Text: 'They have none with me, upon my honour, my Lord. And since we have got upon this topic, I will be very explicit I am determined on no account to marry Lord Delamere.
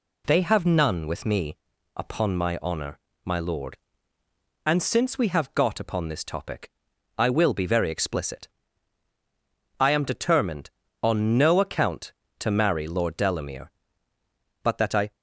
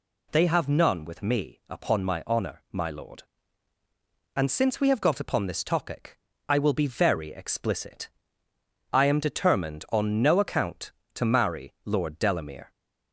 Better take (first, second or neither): second